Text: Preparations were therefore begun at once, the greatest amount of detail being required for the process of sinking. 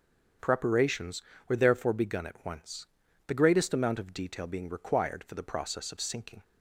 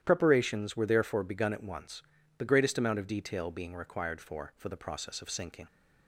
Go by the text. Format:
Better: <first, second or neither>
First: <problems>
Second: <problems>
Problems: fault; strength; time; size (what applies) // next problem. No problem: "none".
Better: first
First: starts louder than the rest; strong; until 1.7 s; 7.5 dB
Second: starts louder than the rest; strong; until 1.0 s; 11 dB // says "for" twice; at 4.5 s